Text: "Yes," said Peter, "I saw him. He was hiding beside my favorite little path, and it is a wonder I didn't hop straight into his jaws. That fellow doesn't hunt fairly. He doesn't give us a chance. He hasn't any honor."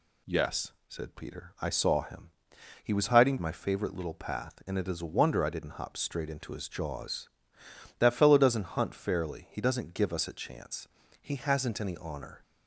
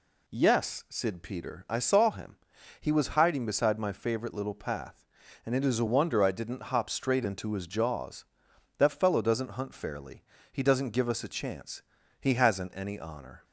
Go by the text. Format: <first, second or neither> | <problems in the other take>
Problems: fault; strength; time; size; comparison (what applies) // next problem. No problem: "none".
second | skips "beside"; at 3.3 s